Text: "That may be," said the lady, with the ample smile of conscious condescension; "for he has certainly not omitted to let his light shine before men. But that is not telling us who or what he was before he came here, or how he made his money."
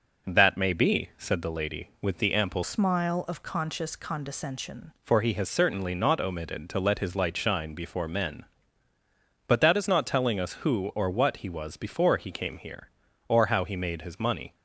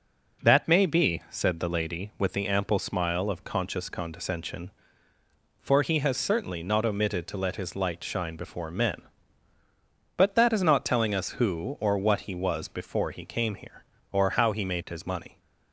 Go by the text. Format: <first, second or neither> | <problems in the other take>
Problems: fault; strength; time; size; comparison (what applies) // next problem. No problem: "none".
second | changes voice from "smile" to "condescension"; from 2.6 to 4.9 s; 2.3 s long